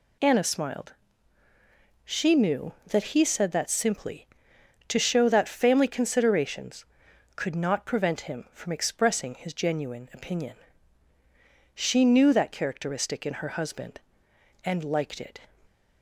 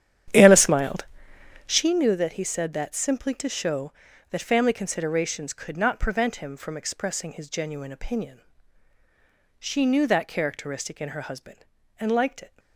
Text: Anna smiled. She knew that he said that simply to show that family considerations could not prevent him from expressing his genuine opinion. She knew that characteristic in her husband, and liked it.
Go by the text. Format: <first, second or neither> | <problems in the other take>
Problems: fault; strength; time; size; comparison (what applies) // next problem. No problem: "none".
first | starts louder than the rest; strong; until 1.9 s; 10 dB